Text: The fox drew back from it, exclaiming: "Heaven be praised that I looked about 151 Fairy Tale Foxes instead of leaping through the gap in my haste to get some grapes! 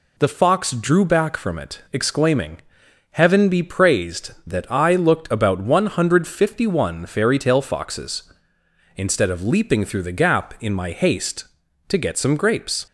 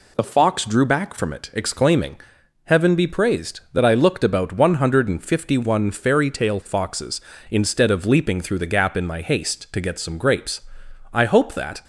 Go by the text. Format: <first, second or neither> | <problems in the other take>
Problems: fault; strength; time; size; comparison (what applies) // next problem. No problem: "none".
first | goes on to say "I hope that"; noticeable; from 11.1 s on; 0.70 s long